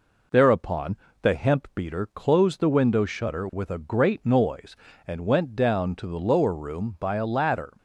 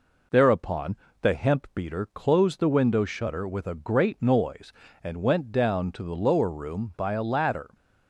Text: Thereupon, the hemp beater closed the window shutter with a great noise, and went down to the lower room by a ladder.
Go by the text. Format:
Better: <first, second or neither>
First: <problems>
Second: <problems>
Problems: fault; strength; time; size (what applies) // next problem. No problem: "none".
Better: neither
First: none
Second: none